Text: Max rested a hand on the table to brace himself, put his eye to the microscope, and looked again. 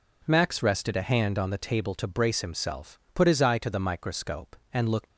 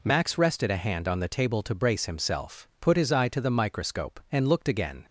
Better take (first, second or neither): second